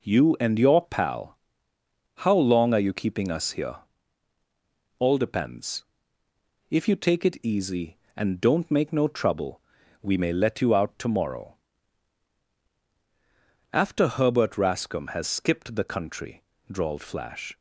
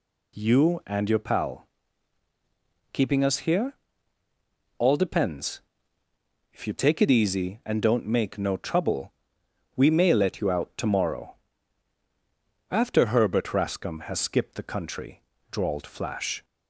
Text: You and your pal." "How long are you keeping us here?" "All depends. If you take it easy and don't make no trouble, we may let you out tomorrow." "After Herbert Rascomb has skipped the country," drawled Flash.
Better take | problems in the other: first | skips "How long are you"; at 2.3 s

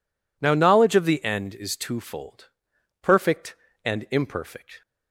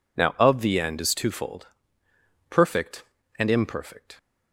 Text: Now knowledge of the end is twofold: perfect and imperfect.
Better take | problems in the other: first | skips "knowledge"; at 0.3 s

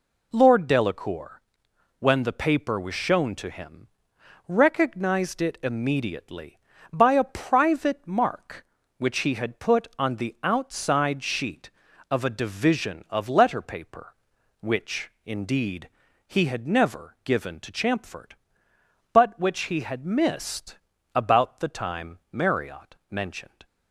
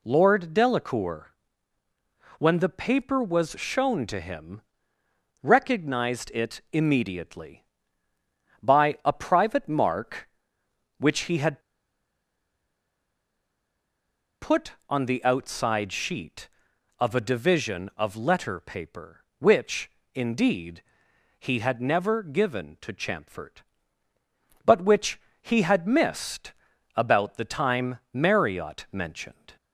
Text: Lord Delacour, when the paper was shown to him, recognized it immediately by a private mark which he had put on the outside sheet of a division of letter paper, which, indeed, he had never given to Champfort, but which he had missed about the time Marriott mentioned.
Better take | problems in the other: first | pauses between "had" and "put"; strong; at 11.6 s; 2.8 s long // pauses between "which" and "he"; slight; at 25.2 s; 0.22 s long // pauses between "missed" and "about"; at 26.5 s; 0.42 s long; also in the first // pauses between "time" and "Marriott"; slight; at 27.9 s; 0.16 s long

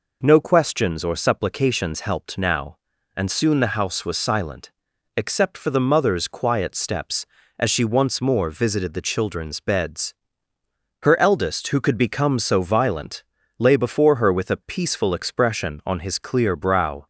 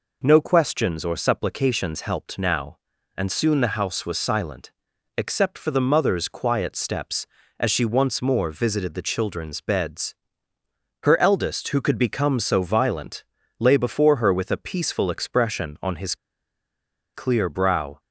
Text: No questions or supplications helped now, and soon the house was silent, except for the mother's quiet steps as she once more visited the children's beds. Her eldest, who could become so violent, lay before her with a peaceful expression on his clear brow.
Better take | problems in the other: first | pauses between "his" and "clear"; at 16.1 s; 0.99 s long

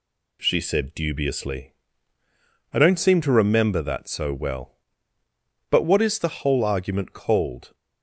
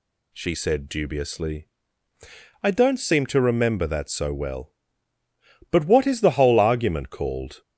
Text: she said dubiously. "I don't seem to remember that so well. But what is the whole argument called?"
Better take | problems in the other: neither | none

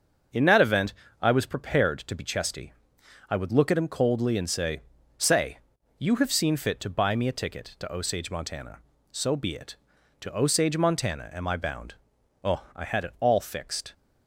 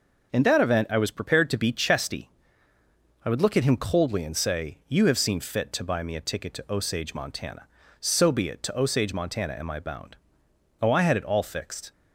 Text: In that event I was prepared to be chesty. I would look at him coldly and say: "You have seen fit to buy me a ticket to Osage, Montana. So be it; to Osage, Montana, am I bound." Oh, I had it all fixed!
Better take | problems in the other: second | starts louder than the rest; until 1.6 s; 7 dB // pauses between "event" and "I"; slight; at 0.9 s; 0.28 s long // says "say" twice; at 5.1 s

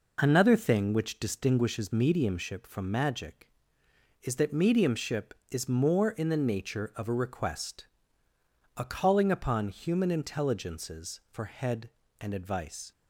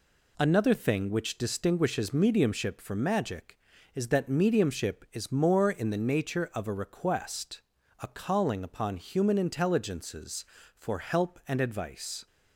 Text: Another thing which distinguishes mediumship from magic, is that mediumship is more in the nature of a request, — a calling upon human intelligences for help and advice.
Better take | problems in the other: second | says "head" for "help"; at 11.4 s

